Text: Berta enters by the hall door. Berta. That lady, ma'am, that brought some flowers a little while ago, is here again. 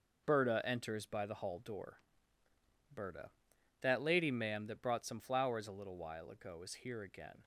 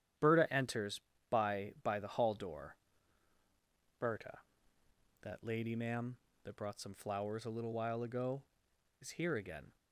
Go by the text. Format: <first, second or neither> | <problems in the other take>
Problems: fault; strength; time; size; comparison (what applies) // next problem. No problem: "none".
first | starts louder than the rest; strong; until 1.4 s; 10 dB // says "by" twice; at 1.8 s